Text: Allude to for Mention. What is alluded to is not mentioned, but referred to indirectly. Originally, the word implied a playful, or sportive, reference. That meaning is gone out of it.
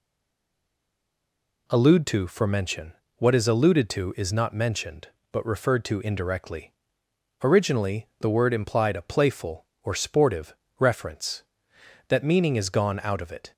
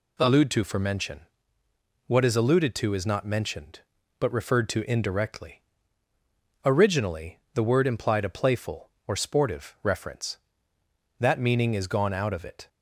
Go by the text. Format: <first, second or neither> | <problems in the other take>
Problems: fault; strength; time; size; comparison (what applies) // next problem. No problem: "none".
second | stays silent before the first word; noticeable; until 1.6 s; 1.6 s long